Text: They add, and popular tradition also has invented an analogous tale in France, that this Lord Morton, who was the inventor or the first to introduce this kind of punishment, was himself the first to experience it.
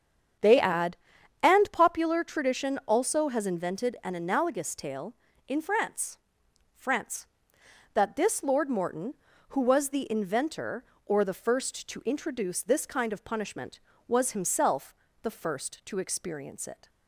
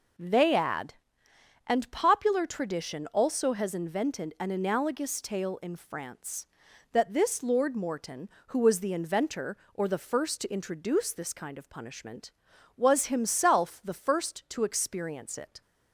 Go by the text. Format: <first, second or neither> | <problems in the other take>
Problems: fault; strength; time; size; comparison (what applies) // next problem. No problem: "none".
second | starts louder than the rest; strong; until 1.8 s; 8 dB // says "France" twice; at 6.7 s // pauses between "himself" and "the"; slight; at 14.9 s; 0.28 s long